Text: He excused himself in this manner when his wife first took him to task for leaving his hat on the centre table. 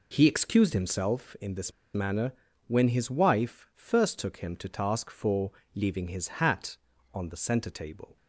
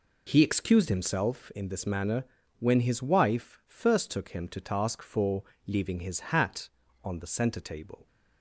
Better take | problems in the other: second | pauses between "this" and "manner"; slight; at 1.7 s; 0.22 s long // pauses between "manner" and "when"; slight; at 2.3 s; 0.34 s long; slight in the second // pauses between "for" and "leaving"; slight; at 5.5 s; 0.24 s long; slight in the second

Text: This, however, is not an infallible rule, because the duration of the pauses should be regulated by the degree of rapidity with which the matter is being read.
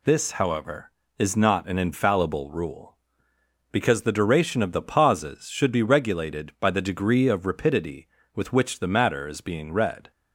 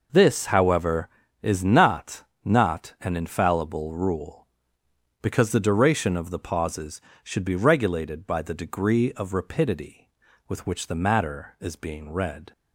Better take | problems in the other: first | says "not" twice; at 2.4 s

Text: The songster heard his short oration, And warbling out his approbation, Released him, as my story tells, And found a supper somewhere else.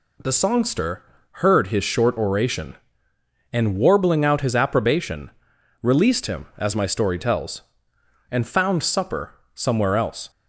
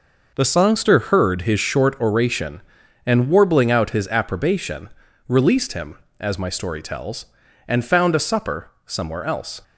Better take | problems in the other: second | pauses between "songster" and "heard"; slight; at 1.0 s; 0.28 s long // skips "a"; at 8.8 s // pauses between "supper" and "somewhere"; slight; at 9.3 s; 0.20 s long

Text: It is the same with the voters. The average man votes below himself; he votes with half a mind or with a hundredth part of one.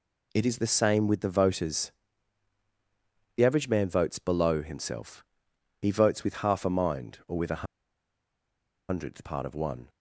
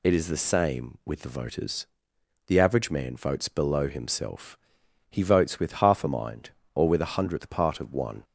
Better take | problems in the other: second | pauses between "a" and "hundredth"; at 7.6 s; 1.2 s long

